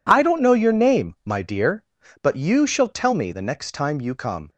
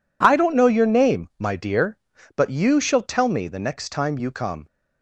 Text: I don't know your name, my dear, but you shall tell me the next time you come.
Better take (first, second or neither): neither